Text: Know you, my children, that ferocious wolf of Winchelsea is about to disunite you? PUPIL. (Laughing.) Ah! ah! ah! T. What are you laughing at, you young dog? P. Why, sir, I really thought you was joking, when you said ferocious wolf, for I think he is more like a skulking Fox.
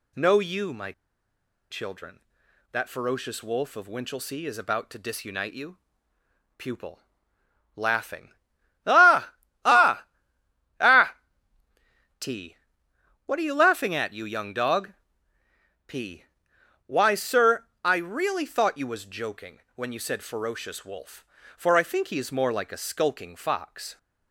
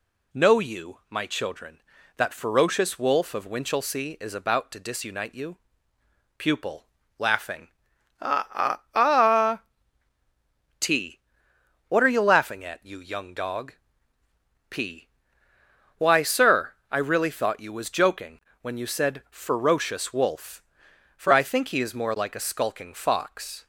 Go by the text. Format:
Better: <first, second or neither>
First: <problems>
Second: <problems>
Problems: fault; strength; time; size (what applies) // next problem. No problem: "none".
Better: second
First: pauses between "my" and "children"; noticeable; at 0.9 s; 0.79 s long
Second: none